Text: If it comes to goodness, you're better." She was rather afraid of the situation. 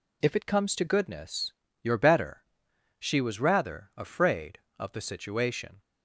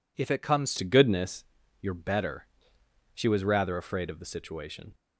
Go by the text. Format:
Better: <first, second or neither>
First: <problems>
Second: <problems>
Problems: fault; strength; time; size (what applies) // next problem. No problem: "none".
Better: first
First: none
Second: changes voice at "to"; from 0.7 s on; 4.2 s long